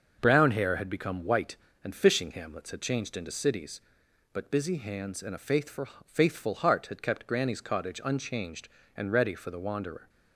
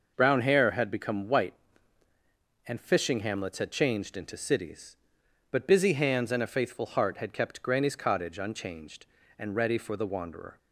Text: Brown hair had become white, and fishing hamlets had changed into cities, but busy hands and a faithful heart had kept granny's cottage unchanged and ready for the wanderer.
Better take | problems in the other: second | starts louder than the rest; until 1.2 s; 6.5 dB // says "faithful" twice; at 6.0 s

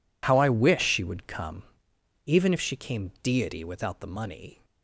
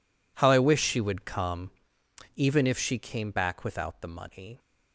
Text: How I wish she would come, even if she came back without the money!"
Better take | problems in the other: second | says "deity" for "back"; at 3.2 s

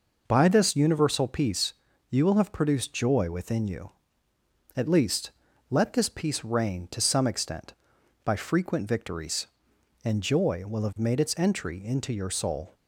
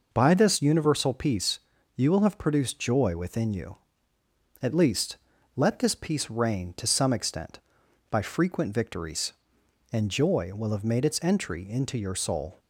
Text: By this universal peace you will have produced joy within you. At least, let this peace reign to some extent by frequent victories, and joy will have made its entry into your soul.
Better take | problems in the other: neither | pauses between "peace" and "you"; slight; the same in both

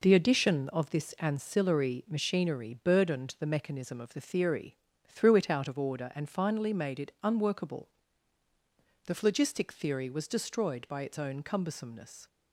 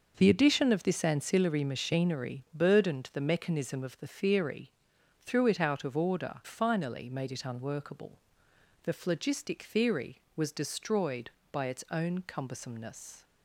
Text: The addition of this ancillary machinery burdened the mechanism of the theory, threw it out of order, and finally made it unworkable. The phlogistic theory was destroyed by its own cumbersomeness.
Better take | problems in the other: first | skips "and"; at 6.4 s

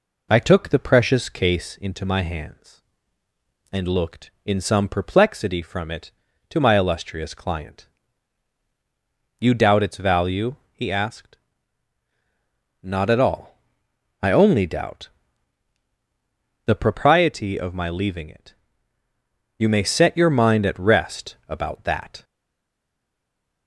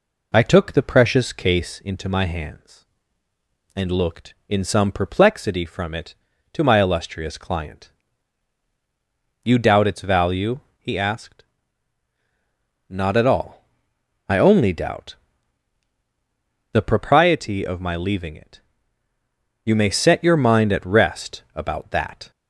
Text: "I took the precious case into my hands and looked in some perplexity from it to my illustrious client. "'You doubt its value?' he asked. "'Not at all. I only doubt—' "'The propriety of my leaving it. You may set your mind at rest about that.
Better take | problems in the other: second | stays silent after the last word; noticeable; from 22.2 s on; 1.4 s long

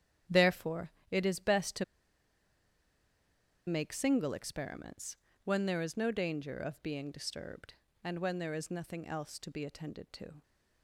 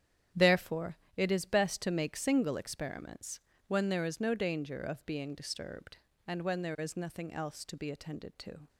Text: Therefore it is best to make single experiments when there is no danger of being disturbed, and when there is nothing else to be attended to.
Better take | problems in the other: second | starts louder than the rest; strong; until 1.4 s; 9.5 dB; strong in the second // pauses between "Therefore" and "it"; slight; at 0.9 s; 0.18 s long; slight in the second // pauses between "to" and "make"; strong; at 1.8 s; 1.8 s long // pauses between "experiments" and "when"; slight; at 5.1 s; 0.28 s long; slight in the second

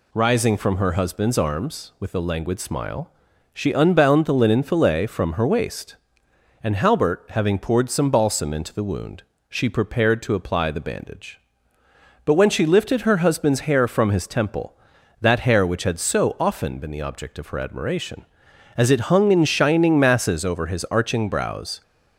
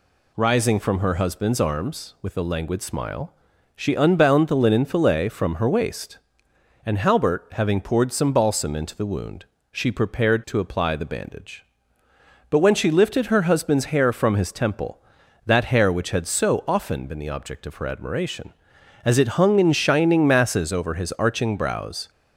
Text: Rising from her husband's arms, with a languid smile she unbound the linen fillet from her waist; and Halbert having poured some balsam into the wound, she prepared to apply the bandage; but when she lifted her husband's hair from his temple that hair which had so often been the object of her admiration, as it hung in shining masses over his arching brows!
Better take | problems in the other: neither | pauses between "smile" and "she"; the same in both

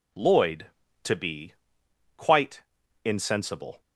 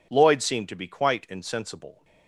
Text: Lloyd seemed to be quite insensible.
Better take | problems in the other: second | skips "seemed"; at 0.8 s // pauses between "be" and "quite"; noticeable; at 1.5 s; 0.64 s long // pauses between "quite" and "insensible"; at 2.6 s; 0.42 s long

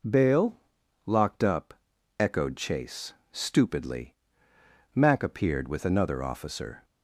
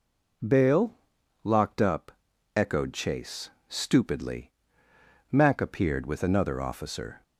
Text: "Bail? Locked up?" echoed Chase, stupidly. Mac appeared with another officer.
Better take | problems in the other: neither | none

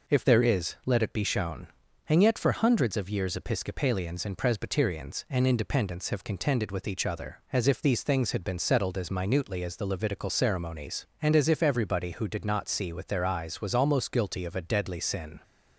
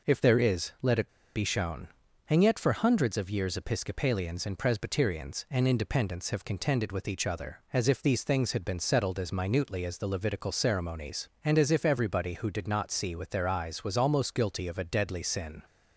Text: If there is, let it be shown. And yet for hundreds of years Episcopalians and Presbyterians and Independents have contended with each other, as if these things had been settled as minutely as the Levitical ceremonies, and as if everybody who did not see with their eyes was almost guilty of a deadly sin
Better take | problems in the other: first | pauses between "it" and "be"; slight; at 1.0 s; 0.25 s long

